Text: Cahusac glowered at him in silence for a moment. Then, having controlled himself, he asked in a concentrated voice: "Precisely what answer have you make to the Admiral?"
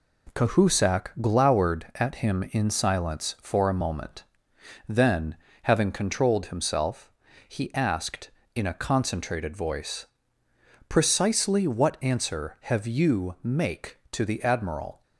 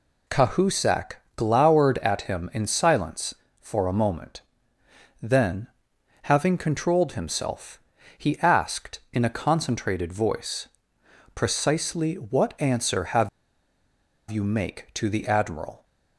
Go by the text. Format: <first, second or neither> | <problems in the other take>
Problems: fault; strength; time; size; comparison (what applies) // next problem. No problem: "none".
first | pauses between "Cahusac" and "glowered"; slight; at 1.1 s; 0.20 s long // pauses between "have" and "you"; at 13.2 s; 1.0 s long